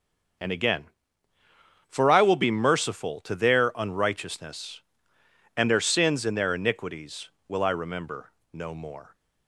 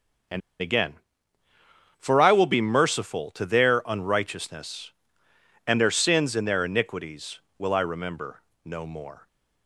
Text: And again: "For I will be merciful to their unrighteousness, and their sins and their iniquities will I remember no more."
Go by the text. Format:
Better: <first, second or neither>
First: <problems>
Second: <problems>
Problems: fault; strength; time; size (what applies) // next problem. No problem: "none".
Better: first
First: starts louder than the rest; until 2.4 s; 6 dB // pauses between "remember" and "no"; slight; at 8.3 s; 0.20 s long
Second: starts louder than the rest; until 2.5 s; 6 dB // pauses between "And" and "again"; slight; at 0.4 s; 0.20 s long // pauses between "remember" and "no"; slight; at 8.4 s; 0.22 s long